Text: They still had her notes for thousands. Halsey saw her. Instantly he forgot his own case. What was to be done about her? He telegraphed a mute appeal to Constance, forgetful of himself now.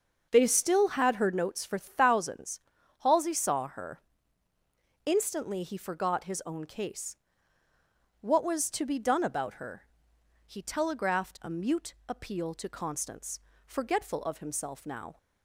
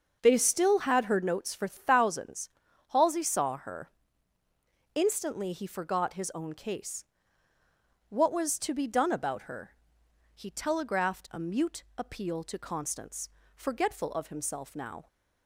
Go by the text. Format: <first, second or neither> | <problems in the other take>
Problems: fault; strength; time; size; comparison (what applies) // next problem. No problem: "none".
neither | starts louder than the rest; the same in both // pauses between "mute" and "appeal"; slight; the same in both